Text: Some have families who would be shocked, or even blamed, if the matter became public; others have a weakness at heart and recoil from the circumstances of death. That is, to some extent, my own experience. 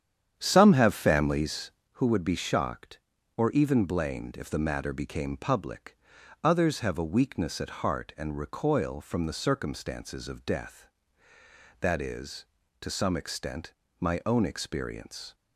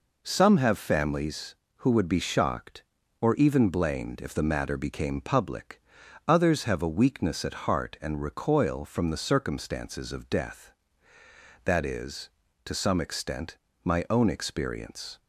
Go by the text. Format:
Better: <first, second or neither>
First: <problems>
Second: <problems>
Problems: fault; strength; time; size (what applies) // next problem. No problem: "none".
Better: second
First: starts louder than the rest; strong; until 1.9 s; 9 dB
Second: none